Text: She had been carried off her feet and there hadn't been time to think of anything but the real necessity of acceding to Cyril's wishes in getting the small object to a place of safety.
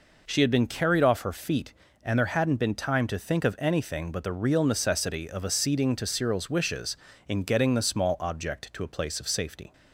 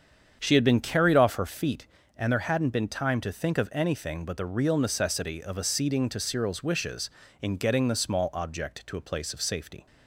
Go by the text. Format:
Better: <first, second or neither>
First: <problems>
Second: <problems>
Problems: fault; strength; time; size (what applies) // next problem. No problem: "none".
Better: first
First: none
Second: starts louder than the rest; strong; until 1.7 s; 7.5 dB